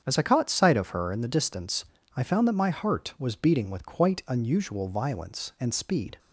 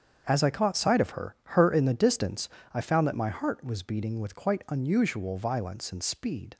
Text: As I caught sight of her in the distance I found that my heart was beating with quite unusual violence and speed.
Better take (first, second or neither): first